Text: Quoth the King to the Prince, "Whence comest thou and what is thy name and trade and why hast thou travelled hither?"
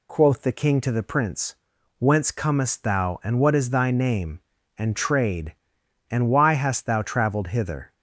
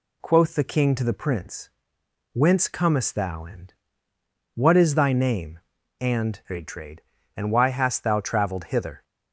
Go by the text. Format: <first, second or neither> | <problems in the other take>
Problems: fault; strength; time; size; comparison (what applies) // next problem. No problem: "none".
first | pauses between "and" and "what"; noticeable; at 3.7 s; 0.80 s long // says "trade" twice; at 6.6 s